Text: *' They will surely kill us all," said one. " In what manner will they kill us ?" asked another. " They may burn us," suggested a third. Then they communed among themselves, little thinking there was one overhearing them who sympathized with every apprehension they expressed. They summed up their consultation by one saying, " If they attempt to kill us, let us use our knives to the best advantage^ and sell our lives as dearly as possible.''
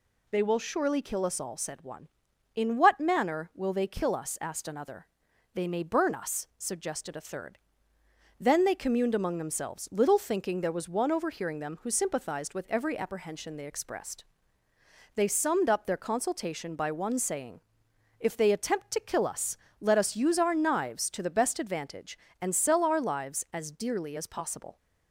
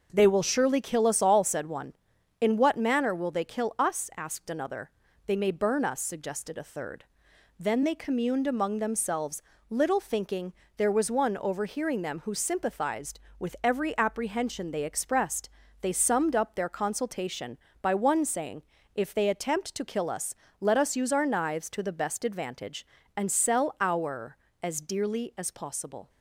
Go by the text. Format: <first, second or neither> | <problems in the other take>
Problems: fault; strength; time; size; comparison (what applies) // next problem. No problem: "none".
first | starts louder than the rest; until 1.1 s; 6 dB // pauses between "thinking" and "there"; slight; at 10.5 s; 0.22 s long // skips "lives"; at 24.4 s